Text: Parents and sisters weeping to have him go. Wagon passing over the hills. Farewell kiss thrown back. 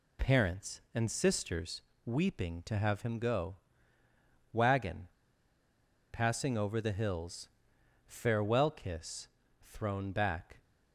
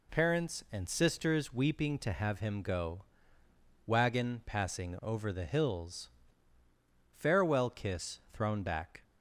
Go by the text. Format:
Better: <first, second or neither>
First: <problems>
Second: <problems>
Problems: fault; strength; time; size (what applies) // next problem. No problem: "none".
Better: second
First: pauses between "sisters" and "weeping"; slight; at 1.8 s; 0.24 s long // pauses between "Wagon" and "passing"; at 5.0 s; 1.0 s long // pauses between "kiss" and "thrown"; at 9.2 s; 0.38 s long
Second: none